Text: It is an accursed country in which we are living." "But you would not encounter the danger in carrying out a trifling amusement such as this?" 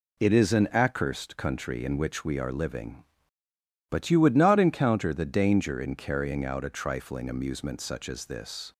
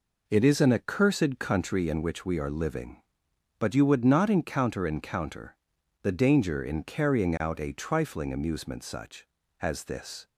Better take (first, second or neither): first